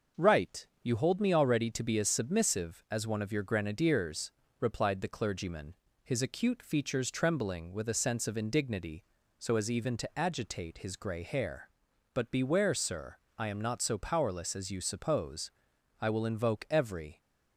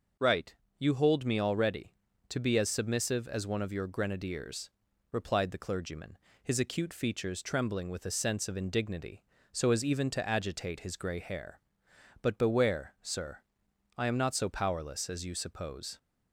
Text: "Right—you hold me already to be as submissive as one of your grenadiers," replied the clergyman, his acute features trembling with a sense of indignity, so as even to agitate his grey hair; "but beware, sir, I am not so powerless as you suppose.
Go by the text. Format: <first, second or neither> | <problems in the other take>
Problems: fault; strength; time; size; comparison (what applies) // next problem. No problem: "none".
second | goes on to say "I will invoke every"; noticeable; from 15.9 s on; 1.2 s long